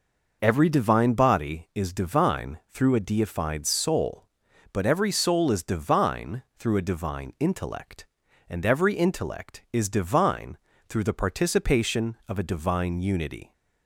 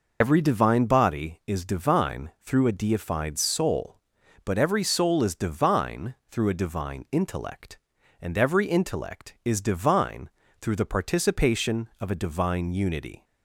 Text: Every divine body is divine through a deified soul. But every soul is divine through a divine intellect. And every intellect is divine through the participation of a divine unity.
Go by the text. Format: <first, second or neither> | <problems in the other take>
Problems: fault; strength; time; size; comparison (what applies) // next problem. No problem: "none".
first | loses the start of "Every"; at 0.2 s; 65 ms // pauses between "divine" and "through"; slight; at 10.2 s; 0.32 s long; slight in the first